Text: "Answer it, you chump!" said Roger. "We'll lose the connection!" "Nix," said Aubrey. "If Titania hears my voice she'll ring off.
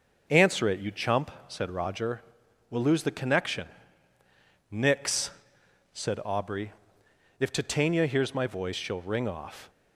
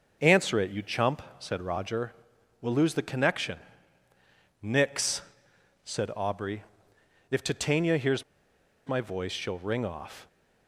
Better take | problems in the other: first | starts louder than the rest; until 1.2 s; 6.5 dB; also in the first // pauses between "hears" and "my"; noticeable; at 8.2 s; 0.65 s long

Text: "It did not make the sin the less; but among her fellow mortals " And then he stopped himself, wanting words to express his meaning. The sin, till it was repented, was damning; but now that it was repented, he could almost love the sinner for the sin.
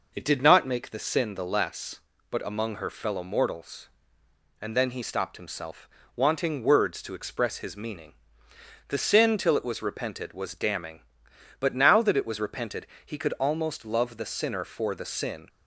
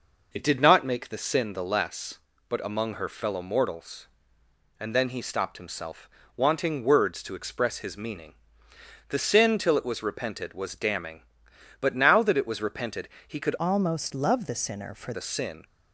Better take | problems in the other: first | changes voice from "almost" to "for"; from 13.5 to 15.1 s; 1.6 s long

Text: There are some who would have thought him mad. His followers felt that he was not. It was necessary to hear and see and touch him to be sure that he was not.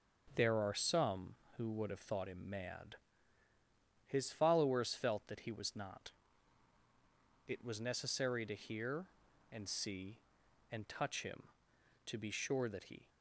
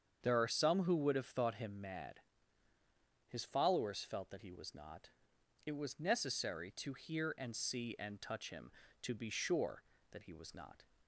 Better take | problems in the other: second | starts louder than the rest; until 1.3 s; 6.5 dB; strong in the second // stops before "was not"; at 13.0 s

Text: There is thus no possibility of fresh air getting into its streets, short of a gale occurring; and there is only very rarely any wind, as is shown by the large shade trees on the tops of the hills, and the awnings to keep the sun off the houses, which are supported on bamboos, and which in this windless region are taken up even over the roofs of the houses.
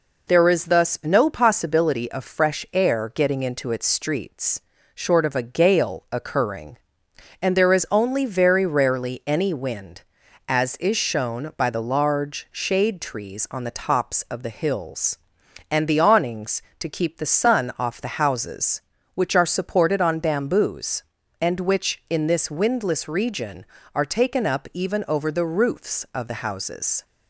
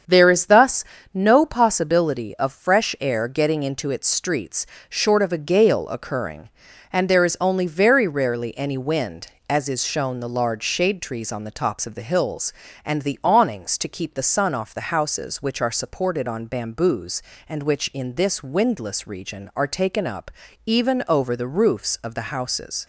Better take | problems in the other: first | starts louder than the rest; strong; until 1.3 s; 7.5 dB // pauses between "thus" and "no"; slight; at 0.8 s; 0.32 s long // skips "by"; at 10.1 s // pauses between "up" and "even"; at 20.2 s; 0.38 s long

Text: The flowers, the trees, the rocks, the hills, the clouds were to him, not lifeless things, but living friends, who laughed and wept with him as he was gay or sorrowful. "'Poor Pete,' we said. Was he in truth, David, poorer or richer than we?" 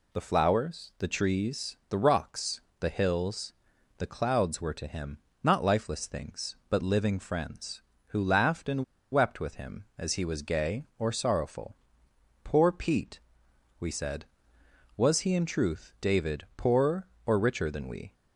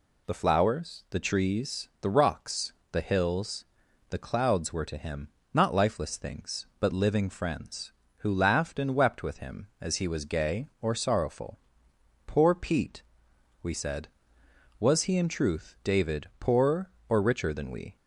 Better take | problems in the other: second | pauses between "and" and "wept"; slight; at 8.8 s; 0.28 s long

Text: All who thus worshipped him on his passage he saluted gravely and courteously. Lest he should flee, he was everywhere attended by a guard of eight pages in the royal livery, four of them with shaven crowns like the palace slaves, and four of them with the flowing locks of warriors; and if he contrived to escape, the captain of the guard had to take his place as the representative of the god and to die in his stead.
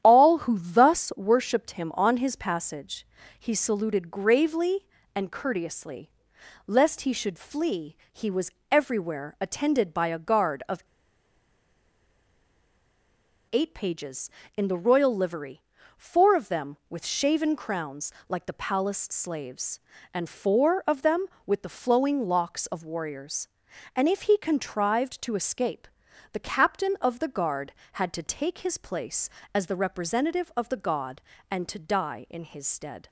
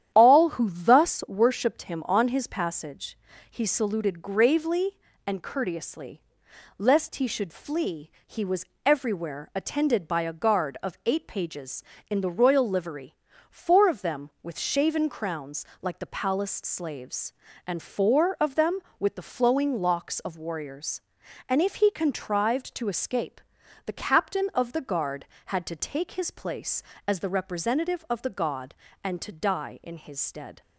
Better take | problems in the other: second | starts louder than the rest; strong; until 1.0 s; 10.5 dB; strong in the second // pauses between "passage" and "he"; slight; at 3.0 s; 0.32 s long; slight in the second // pauses between "was" and "everywhere"; slight; at 8.5 s; 0.20 s long; slight in the second // pauses between "of" and "eight"; strong; at 10.8 s; 2.6 s long // pauses between "crowns" and "like"; slight; at 18.1 s; 0.16 s long; slight in the second

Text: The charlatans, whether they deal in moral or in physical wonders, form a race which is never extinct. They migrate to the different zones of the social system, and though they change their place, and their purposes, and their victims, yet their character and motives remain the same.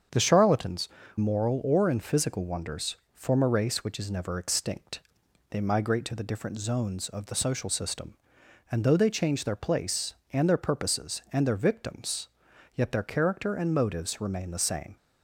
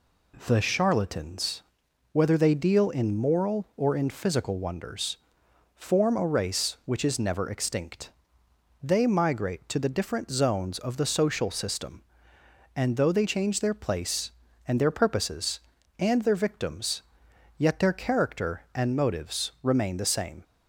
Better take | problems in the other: second | starts louder than the rest; strong; until 1.4 s; 7.5 dB // skips "whether they deal in"; at 1.0 s

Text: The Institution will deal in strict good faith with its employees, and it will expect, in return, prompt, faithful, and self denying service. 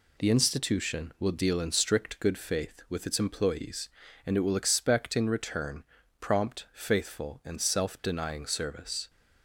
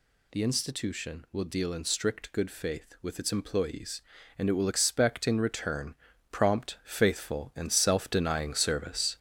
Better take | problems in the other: first | gets louder; noticeable; throughout; 6 dB

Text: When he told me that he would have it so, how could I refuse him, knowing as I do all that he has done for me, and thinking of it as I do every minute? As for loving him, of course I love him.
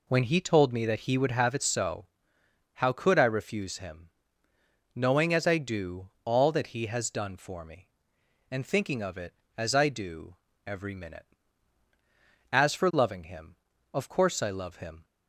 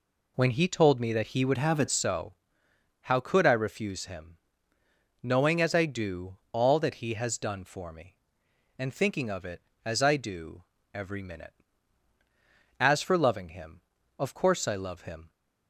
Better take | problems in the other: first | changes voice from "have" to "it"; from 1.5 to 1.8 s; 0.3 s long // pauses between "do" and "all"; slight; at 6.3 s; 0.16 s long; slight in the first // pauses between "do" and "every"; slight; at 10.6 s; 0.32 s long; slight in the first

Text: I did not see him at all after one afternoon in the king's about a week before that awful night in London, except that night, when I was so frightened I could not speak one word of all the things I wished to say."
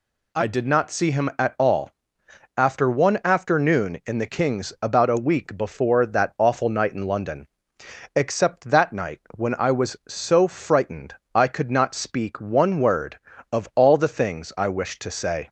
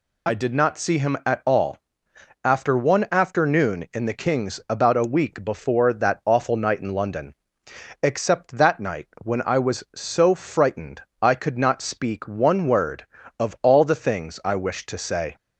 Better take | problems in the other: first | loses the start of "I"; at 0.2 s; 45 ms // pauses between "all" and "after"; noticeable; at 1.7 s; 0.64 s long; noticeable in the first // pauses between "frightened" and "I"; slight; at 11.0 s; 0.20 s long; slight in the first

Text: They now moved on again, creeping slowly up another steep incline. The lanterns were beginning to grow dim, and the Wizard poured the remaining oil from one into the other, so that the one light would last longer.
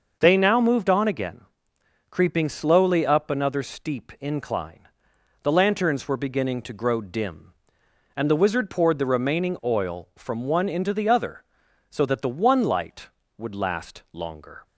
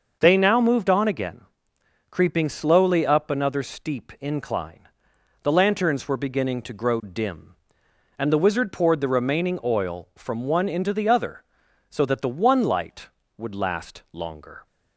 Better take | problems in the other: neither | starts louder than the rest; noticeable; the same in both

